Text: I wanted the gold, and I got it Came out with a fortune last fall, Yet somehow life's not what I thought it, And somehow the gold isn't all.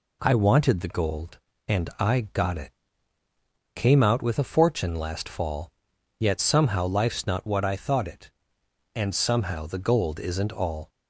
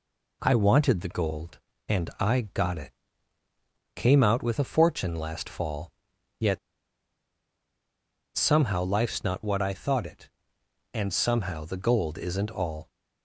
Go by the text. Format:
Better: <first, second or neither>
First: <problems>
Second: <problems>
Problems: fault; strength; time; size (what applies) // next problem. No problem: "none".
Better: first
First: pauses between "it" and "Came"; at 2.7 s; 1.0 s long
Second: pauses between "it" and "Came"; at 2.9 s; 1.0 s long // pauses between "Yet" and "somehow"; strong; at 6.5 s; 1.7 s long